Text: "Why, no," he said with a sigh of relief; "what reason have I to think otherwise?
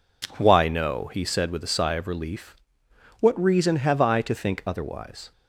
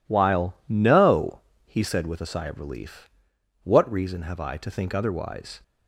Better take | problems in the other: first | says "While" for "Why"; at 0.0 s

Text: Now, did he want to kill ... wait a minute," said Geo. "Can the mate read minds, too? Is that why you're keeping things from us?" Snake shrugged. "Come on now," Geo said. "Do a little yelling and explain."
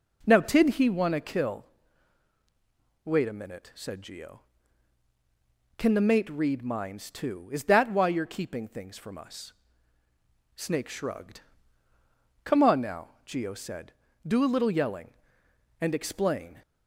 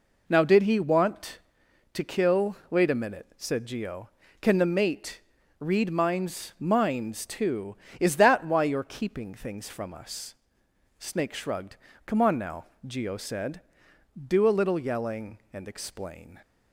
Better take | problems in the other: first | pauses between "mate" and "read"; at 5.1 s; 0.40 s long // says "minds" twice; at 6.5 s

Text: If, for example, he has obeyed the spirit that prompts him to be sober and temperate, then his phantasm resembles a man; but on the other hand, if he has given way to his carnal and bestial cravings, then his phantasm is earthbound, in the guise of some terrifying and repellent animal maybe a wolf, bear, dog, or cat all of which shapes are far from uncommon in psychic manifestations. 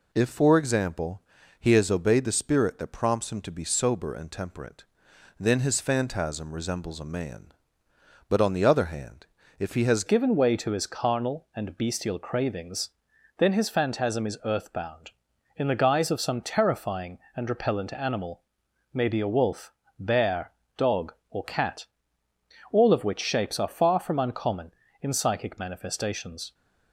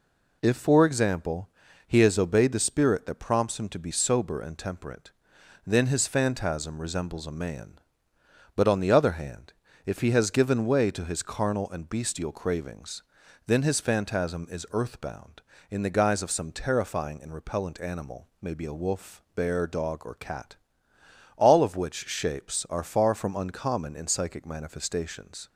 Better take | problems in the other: second | changes voice at "given"; from 10.0 s on; 16.5 s long // pauses between "animal" and "maybe"; noticeable; at 18.4 s; 0.50 s long // pauses between "cat" and "all"; noticeable; at 21.8 s; 0.86 s long; noticeable in the second

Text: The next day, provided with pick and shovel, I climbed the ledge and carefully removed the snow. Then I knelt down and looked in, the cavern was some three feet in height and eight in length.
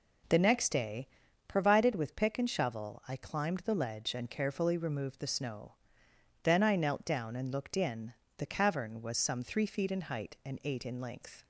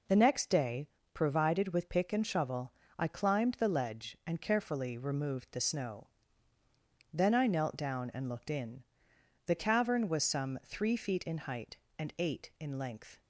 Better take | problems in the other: neither | none

